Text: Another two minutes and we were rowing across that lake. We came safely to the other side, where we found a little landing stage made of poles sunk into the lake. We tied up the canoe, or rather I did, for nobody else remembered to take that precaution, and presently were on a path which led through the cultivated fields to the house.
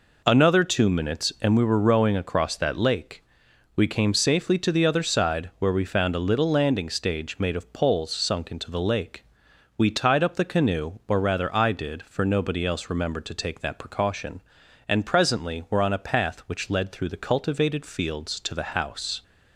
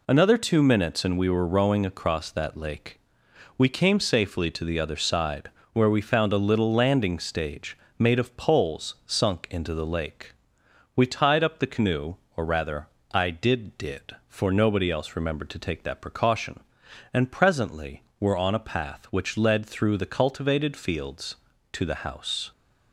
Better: first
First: none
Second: pauses between "stage" and "made"; slight; at 7.7 s; 0.20 s long // pauses between "rather" and "I"; slight; at 12.8 s; 0.24 s long // says "did" twice; at 13.7 s

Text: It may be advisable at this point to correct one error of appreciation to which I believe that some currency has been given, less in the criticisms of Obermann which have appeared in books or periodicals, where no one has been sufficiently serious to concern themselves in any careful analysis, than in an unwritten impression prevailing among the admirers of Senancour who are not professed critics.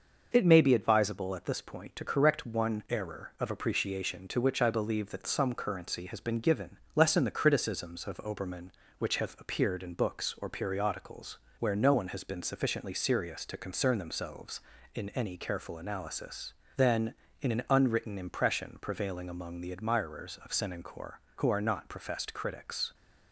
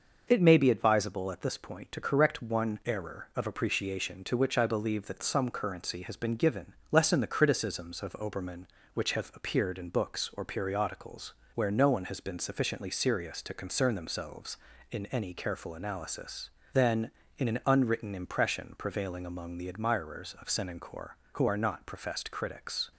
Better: neither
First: starts louder than the rest; until 1.3 s; 6 dB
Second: starts louder than the rest; until 1.2 s; 6 dB

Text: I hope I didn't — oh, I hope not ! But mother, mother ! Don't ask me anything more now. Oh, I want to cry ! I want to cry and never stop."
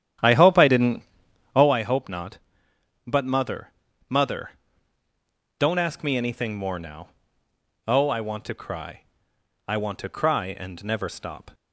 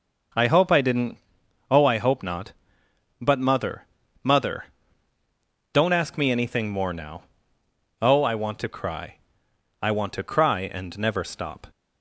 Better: second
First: starts louder than the rest; strong; until 1.7 s; 10.5 dB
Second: none

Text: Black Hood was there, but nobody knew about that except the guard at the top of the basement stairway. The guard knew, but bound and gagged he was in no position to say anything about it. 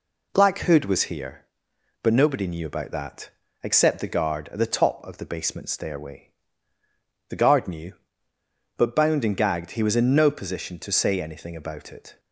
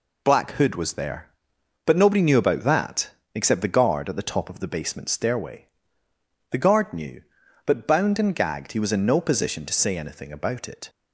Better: second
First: says "here" for "there"; at 1.0 s // pauses between "that" and "except"; slight; at 3.2 s; 0.32 s long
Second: pauses between "that" and "except"; slight; at 3.0 s; 0.24 s long

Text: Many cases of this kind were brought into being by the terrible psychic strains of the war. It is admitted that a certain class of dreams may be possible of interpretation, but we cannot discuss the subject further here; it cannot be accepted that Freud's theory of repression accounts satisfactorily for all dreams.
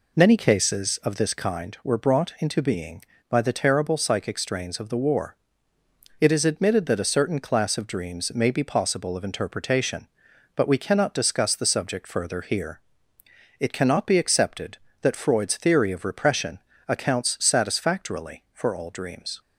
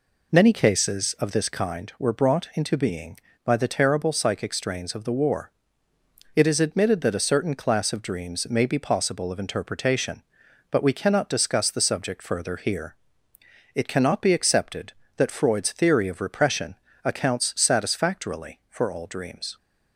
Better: neither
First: pauses between "repression" and "accounts"; slight; at 16.5 s; 0.30 s long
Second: pauses between "repression" and "accounts"; slight; at 16.7 s; 0.30 s long

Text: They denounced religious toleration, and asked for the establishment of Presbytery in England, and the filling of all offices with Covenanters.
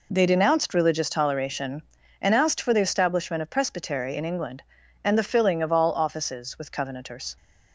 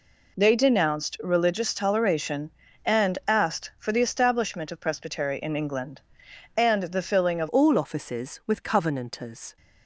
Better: first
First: none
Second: changes voice at "all"; from 7.4 s on; 2.1 s long

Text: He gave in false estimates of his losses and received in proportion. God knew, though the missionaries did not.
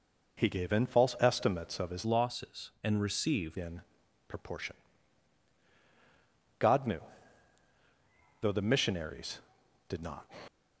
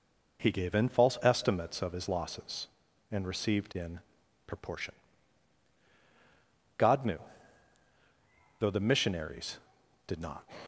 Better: second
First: changes voice from "losses" to "received"; from 2.0 to 3.5 s; 1.5 s long // pauses between "in" and "proportion"; at 3.8 s; 0.44 s long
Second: pauses between "in" and "proportion"; at 4.0 s; 0.44 s long

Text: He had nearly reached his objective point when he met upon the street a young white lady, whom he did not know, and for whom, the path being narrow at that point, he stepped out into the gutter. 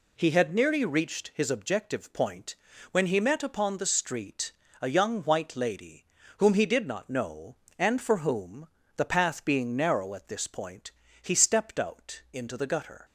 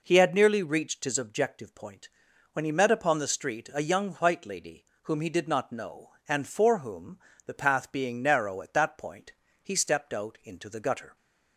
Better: second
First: pauses between "point" and "when"; slight; at 2.5 s; 0.36 s long // pauses between "street" and "a"; slight; at 4.5 s; 0.30 s long // says "this" for "that"; at 10.2 s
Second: pauses between "point" and "when"; at 2.0 s; 0.42 s long

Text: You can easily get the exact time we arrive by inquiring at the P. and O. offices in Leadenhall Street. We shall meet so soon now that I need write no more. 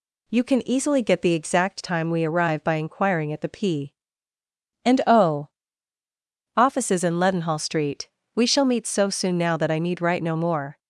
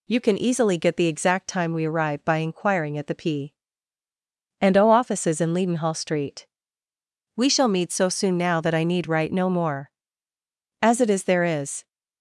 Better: first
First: none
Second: goes on to say "As it is there is"; noticeable; from 10.8 s on; 1.0 s long

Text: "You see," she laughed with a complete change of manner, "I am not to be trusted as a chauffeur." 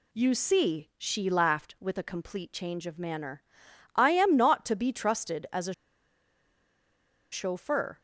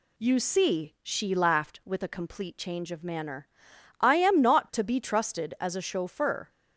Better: second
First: pauses between "a" and "chauffeur"; strong; at 5.7 s; 1.5 s long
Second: none

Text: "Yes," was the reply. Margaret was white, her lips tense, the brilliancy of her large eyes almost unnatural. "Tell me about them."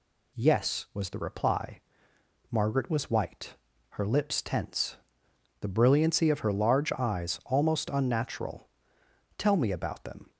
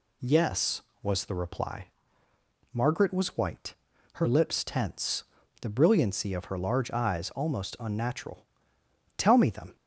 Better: first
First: none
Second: skips "about"; at 9.4 s

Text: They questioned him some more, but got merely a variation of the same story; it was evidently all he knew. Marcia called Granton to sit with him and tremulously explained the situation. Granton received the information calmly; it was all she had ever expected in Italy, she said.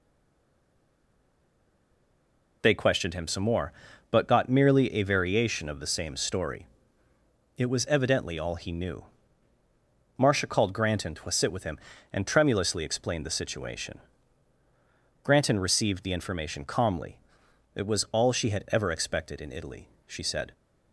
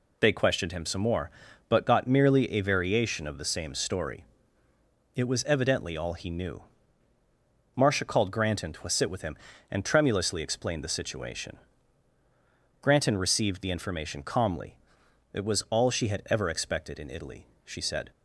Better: second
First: stays silent before the first word; strong; until 2.6 s; 2.6 s long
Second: none

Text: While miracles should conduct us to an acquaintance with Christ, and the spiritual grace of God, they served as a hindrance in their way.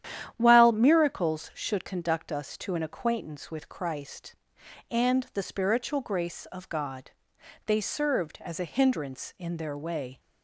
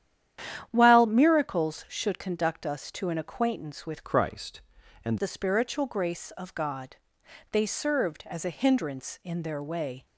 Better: first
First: starts louder than the rest; strong; until 1.3 s; 10.5 dB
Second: starts louder than the rest; strong; until 1.7 s; 10 dB // changes voice from "Christ" to "and"; from 4.0 to 5.1 s; 1.1 s long

